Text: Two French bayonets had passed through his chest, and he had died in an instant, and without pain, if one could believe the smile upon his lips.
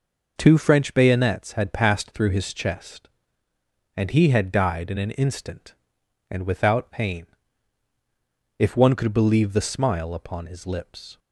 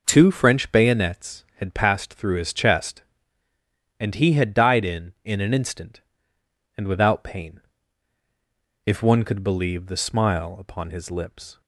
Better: first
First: none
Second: says "in" twice; at 5.2 s

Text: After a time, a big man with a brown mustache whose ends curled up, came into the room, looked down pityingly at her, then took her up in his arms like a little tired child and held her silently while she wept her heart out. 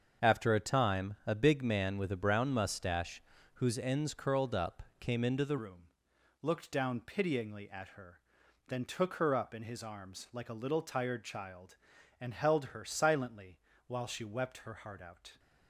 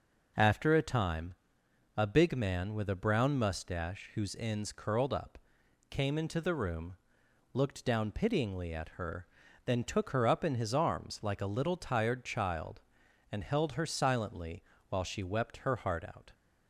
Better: second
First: starts louder than the rest; until 1.3 s; 7 dB // pauses between "mustache" and "whose"; slight; at 3.2 s; 0.34 s long // changes voice at "room"; from 5.5 s on; 9.8 s long // pauses between "silently" and "while"; slight; at 13.5 s; 0.30 s long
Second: pauses between "silently" and "while"; slight; at 14.6 s; 0.26 s long

